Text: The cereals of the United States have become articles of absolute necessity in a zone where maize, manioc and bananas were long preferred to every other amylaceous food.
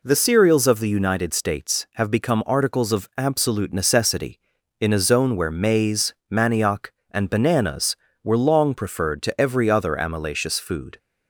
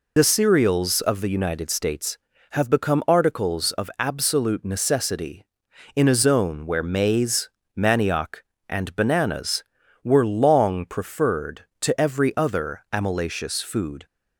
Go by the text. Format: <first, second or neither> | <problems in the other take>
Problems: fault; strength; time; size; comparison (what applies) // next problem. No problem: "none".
first | loses the start of "The"; at 0.1 s; 70 ms